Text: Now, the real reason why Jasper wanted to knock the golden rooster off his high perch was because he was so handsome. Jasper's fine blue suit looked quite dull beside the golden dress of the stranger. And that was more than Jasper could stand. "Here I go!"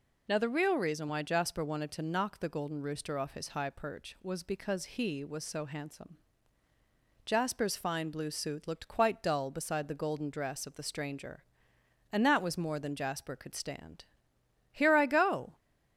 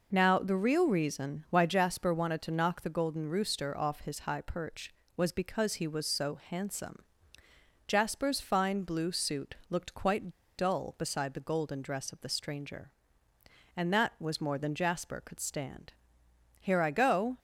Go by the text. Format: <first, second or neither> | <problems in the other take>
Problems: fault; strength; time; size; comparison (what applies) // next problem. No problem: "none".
first | pauses between "quite" and "dull"; slight; at 10.3 s; 0.25 s long